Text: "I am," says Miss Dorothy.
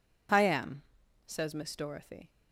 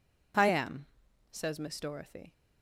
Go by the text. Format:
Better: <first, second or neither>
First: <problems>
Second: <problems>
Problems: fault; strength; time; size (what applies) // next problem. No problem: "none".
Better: neither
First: none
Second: none